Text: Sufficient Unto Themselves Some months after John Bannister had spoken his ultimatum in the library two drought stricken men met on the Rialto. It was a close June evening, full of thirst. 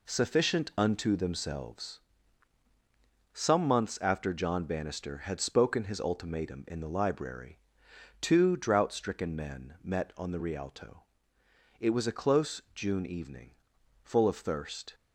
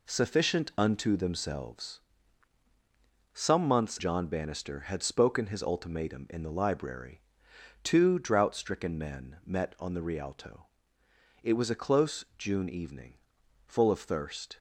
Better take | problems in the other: first | pauses between "Themselves" and "Some"; strong; at 1.9 s; 1.3 s long; strong in the first // skips "after"; at 3.9 s // pauses between "library" and "two"; noticeable; at 7.1 s; 0.64 s long; noticeable in the first

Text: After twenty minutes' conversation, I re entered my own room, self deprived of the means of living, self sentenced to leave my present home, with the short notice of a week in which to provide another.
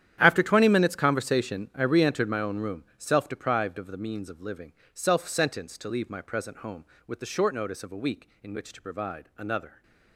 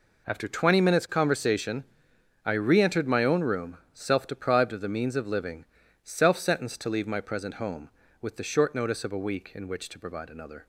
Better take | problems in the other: second | gets quieter; strong; throughout; 16 dB

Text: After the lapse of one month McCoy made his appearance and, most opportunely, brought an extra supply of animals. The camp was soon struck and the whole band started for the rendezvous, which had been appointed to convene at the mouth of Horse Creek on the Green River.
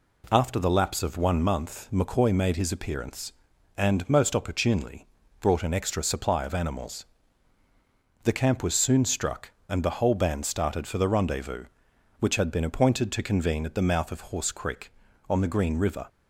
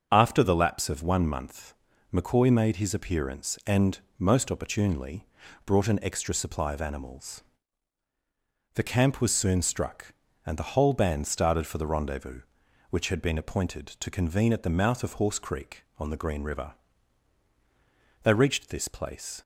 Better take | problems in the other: first | starts louder than the rest; until 1.1 s; 6.5 dB // pauses between "month" and "McCoy"; at 1.7 s; 0.40 s long // goes on to say "They reached this place"; noticeable; from 18.2 s on; 1.2 s long

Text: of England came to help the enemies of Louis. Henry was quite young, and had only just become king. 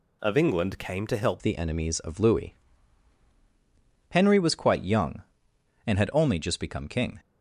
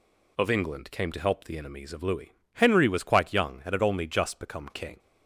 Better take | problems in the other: second | changes voice at "the"; from 1.3 s on; 5.8 s long

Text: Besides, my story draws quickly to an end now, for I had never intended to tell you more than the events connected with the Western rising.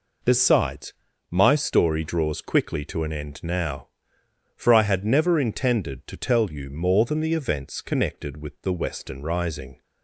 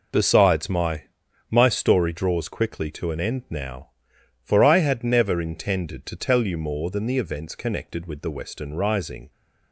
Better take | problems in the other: first | says "my" twice; at 1.5 s

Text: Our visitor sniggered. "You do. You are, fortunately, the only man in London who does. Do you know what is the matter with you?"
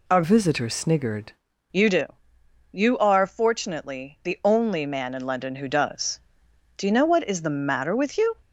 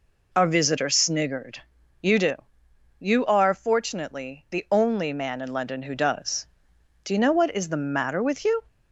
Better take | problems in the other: second | changes voice from "visitor" to "sniggered"; from 0.2 to 1.3 s; 1.1 s long

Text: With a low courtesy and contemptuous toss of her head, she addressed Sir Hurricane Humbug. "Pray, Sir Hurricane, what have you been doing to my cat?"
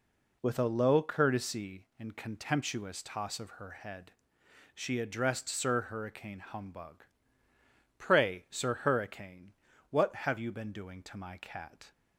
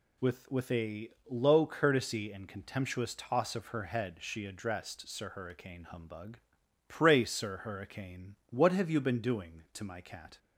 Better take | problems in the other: first | says "With" twice; at 0.4 s // pauses between "a" and "low"; slight; at 1.0 s; 0.20 s long

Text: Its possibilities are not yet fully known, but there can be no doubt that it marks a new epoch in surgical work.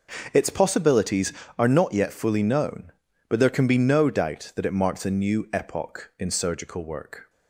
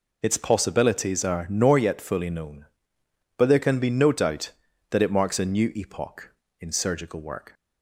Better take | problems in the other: first | says "nor" for "not"; at 1.4 s

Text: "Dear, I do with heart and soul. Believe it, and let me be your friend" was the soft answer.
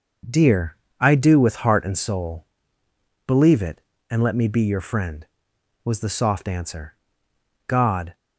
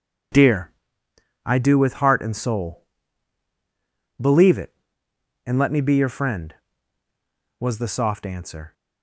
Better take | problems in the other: second | starts louder than the rest; noticeable; until 1.5 s; 6 dB // goes on to say "God"; slight; from 7.6 s on; 0.48 s long

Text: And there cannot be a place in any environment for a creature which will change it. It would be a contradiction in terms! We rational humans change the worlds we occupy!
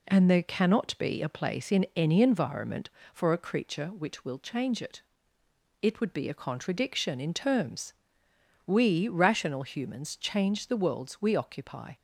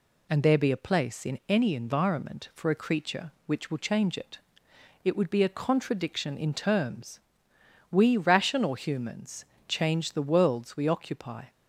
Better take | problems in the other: first | skips "cannot"; at 0.5 s // pauses between "humans" and "change"; slight; at 9.4 s; 0.24 s long

